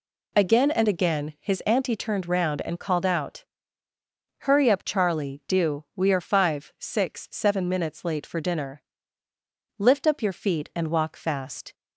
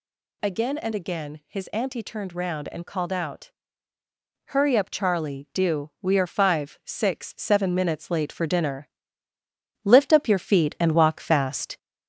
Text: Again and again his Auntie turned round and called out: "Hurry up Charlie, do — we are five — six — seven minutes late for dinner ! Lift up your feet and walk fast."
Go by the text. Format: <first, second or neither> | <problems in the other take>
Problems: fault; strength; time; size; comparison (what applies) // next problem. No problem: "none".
first | gets louder; slight; throughout; 3.5 dB